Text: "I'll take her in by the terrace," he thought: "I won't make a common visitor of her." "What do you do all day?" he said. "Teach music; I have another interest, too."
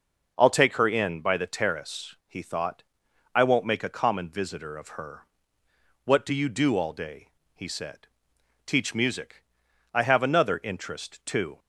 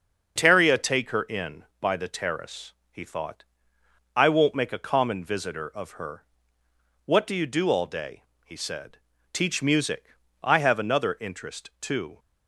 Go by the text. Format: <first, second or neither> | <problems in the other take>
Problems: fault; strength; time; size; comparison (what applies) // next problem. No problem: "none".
first | starts louder than the rest; noticeable; until 1.3 s; 6 dB // says "Teria" for "I'll"; at 0.3 s